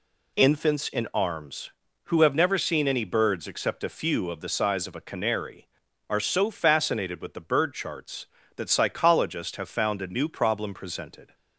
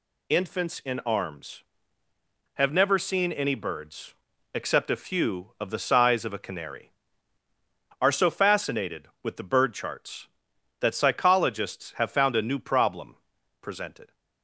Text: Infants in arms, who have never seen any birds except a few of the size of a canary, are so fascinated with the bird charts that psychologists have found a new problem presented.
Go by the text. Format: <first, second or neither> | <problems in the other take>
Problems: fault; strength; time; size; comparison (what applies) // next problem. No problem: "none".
first | skips "who"; at 2.0 s // pauses between "birds" and "except"; at 4.1 s; 0.40 s long // pauses between "problem" and "presented"; at 13.1 s; 0.44 s long